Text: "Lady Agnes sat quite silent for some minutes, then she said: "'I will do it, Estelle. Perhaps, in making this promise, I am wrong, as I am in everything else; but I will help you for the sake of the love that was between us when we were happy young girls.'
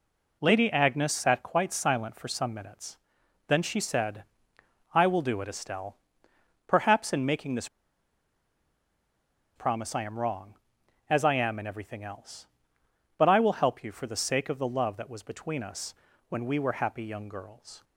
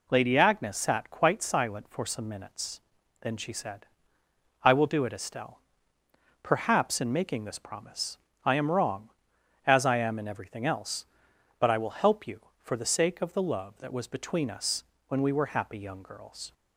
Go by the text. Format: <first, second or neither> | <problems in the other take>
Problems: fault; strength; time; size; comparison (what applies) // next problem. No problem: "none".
second | pauses between "this" and "promise"; strong; at 7.6 s; 1.8 s long // pauses between "us" and "when"; slight; at 15.9 s; 0.34 s long; slight in the second